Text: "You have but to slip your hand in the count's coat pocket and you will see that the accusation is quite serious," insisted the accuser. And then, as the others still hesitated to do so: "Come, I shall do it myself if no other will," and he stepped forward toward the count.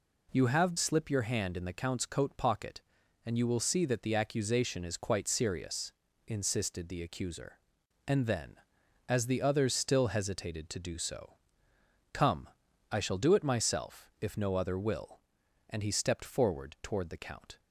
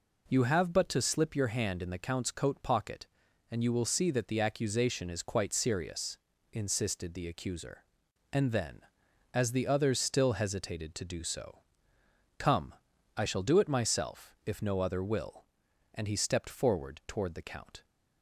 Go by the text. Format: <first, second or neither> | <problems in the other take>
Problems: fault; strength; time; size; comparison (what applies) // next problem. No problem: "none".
second | skips "but to"; at 0.7 s